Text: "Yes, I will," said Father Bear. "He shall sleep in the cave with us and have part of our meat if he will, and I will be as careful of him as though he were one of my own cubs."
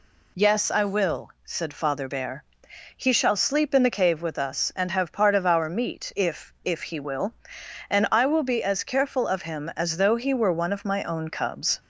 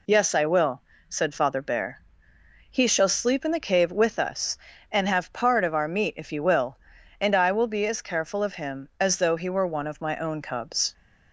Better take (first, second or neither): second